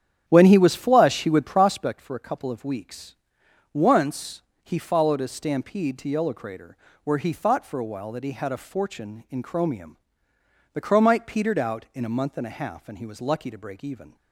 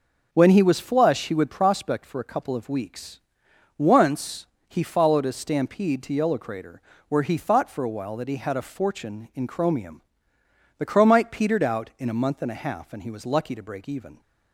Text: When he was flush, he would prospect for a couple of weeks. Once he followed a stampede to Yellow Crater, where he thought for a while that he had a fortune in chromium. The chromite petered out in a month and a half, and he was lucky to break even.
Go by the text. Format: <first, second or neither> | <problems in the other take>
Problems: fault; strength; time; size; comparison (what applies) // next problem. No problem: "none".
second | starts louder than the rest; strong; until 1.9 s; 9 dB // pauses between "Once" and "he"; slight; at 4.4 s; 0.24 s long; slight in the second